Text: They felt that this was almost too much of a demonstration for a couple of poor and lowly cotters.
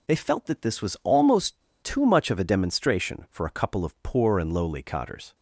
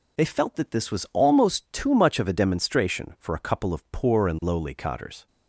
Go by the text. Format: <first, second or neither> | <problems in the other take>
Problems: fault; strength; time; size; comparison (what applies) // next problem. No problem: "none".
second | pauses between "almost" and "too"; slight; at 1.6 s; 0.21 s long